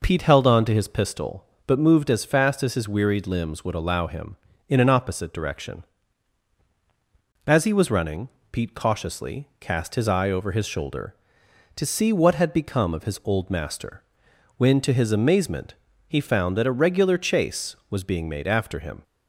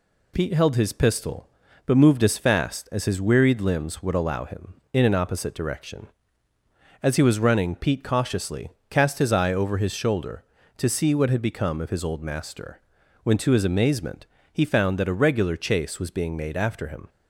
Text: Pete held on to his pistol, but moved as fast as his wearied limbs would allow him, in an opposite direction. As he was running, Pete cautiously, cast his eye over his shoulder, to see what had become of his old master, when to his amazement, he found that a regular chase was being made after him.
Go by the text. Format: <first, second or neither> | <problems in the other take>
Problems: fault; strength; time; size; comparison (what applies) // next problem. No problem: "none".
first | skips "on to"; at 0.7 s